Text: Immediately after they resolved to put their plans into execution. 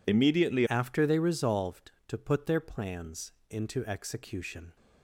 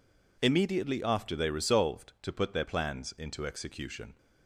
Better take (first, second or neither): second